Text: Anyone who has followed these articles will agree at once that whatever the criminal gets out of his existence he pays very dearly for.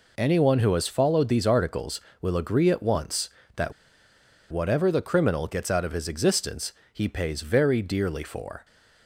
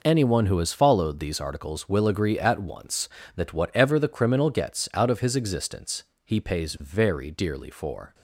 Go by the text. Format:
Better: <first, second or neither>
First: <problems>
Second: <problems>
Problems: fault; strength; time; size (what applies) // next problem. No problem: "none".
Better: second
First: pauses between "that" and "whatever"; noticeable; at 3.7 s; 0.78 s long // pauses between "existence" and "he"; slight; at 6.7 s; 0.20 s long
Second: pauses between "existence" and "he"; slight; at 6.0 s; 0.20 s long